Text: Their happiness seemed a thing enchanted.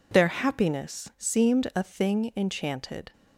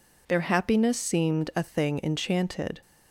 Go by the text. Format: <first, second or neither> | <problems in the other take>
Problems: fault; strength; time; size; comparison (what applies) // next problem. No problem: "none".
neither | none